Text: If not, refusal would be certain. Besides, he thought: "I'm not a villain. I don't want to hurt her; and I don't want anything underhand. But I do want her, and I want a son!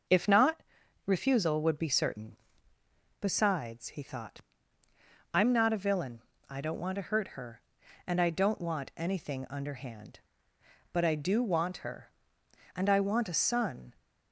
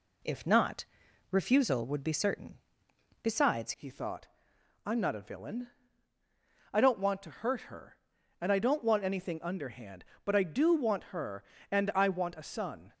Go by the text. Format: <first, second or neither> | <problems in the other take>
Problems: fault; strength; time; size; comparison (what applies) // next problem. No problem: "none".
first | changes voice at "he"; from 3.7 s on; 9.2 s long